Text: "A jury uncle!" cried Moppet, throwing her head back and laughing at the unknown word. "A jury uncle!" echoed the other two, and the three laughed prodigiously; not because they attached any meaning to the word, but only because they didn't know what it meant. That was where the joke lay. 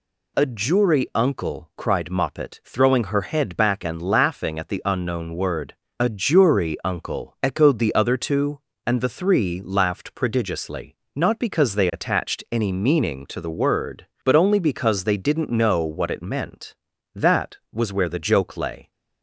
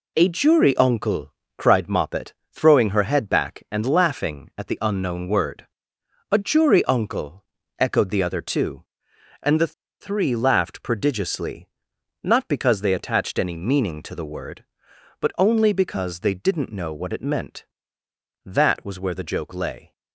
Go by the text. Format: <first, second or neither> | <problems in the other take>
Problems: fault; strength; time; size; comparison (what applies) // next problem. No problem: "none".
first | pauses between "the" and "three"; slight; at 9.7 s; 0.29 s long